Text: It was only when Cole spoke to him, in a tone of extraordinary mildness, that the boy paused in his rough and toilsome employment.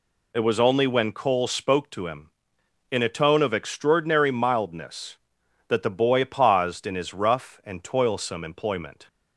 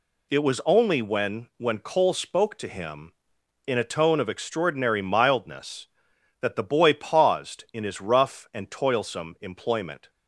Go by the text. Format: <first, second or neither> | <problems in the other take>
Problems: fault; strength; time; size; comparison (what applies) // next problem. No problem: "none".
first | says "when" twice; at 1.5 s